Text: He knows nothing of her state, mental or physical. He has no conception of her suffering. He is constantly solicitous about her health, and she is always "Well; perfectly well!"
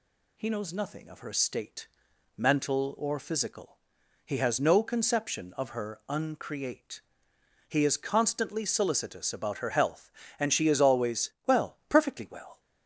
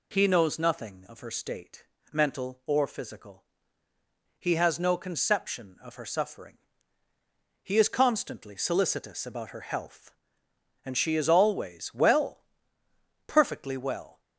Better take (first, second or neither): second